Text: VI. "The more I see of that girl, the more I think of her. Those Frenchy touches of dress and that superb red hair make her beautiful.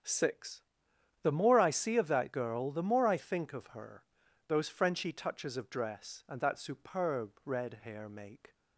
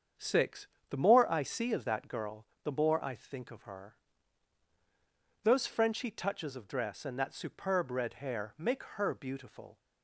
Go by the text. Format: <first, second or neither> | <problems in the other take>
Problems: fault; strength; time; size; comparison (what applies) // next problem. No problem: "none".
second | starts louder than the rest; strong; until 1.6 s; 7.5 dB; strong in the second // stops before "her beautiful"; at 8.5 s